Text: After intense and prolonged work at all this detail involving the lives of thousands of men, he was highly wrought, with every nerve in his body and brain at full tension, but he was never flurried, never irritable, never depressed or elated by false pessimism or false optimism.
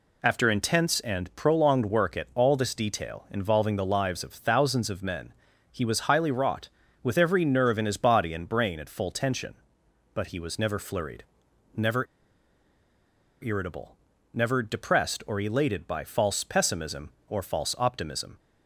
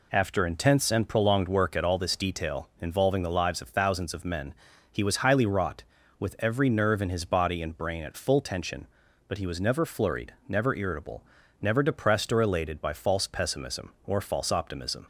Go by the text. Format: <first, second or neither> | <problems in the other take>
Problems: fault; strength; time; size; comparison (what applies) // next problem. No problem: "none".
second | pauses between "never" and "irritable"; strong; at 12.0 s; 1.3 s long